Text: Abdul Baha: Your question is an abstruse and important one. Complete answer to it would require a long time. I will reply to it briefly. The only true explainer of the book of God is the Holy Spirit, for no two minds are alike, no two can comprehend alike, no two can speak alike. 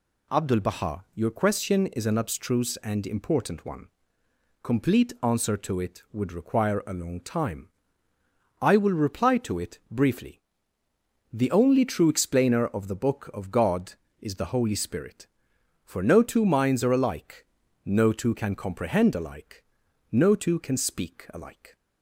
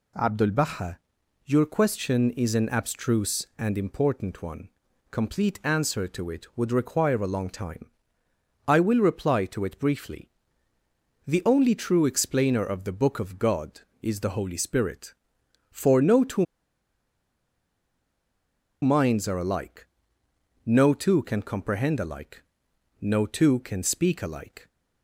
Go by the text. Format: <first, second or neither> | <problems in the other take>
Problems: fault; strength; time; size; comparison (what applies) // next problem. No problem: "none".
first | pauses between "two" and "minds"; strong; at 16.4 s; 2.3 s long